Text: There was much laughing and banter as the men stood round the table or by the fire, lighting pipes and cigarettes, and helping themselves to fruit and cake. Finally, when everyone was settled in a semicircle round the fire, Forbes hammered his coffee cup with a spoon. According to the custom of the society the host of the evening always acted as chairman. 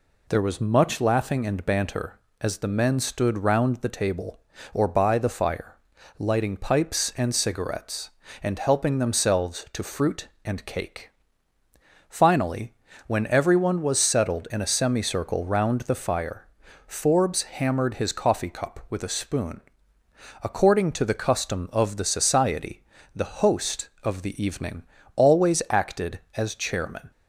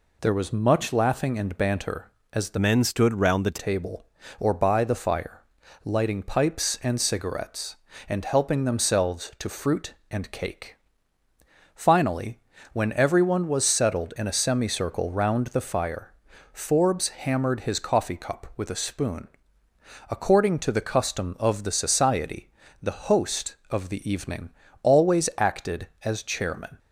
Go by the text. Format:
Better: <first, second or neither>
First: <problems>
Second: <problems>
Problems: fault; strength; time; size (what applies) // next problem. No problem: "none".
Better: first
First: pauses between "society" and "the"; slight; at 22.8 s; 0.34 s long // pauses between "evening" and "always"; slight; at 24.8 s; 0.32 s long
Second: changes voice from "men" to "the"; from 2.5 to 3.5 s; 1.0 s long // pauses between "society" and "the"; slight; at 22.4 s; 0.34 s long // pauses between "evening" and "always"; slight; at 24.4 s; 0.32 s long